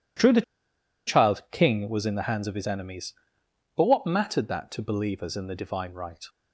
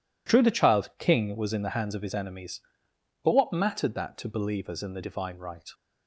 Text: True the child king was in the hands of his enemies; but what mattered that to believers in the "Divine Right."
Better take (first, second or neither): second